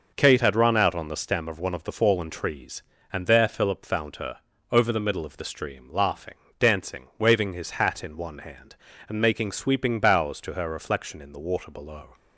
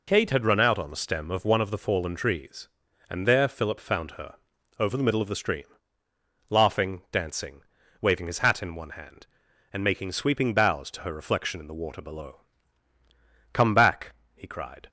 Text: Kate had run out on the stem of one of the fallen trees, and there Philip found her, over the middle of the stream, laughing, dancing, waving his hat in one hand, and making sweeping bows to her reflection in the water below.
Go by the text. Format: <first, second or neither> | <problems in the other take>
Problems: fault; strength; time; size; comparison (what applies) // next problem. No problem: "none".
first | goes on to say "Come back he cried"; from 13.5 s on; 1.3 s long